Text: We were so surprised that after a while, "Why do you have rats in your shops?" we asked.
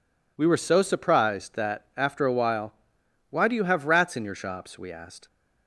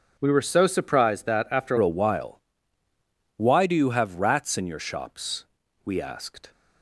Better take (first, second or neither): first